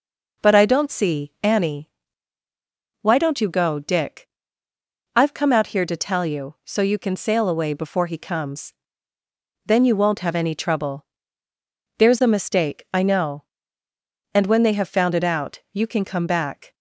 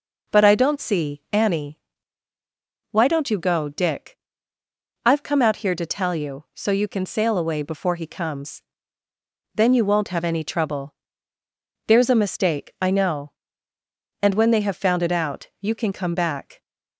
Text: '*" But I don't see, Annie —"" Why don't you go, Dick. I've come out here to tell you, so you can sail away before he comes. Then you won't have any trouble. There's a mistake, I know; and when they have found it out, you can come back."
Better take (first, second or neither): neither